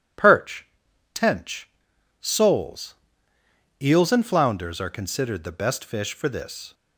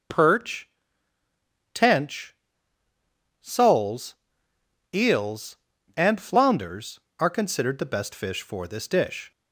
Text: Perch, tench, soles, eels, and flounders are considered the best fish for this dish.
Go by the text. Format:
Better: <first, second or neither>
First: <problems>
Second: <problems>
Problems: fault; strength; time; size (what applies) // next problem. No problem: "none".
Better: second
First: stops before "dish"; at 6.7 s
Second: none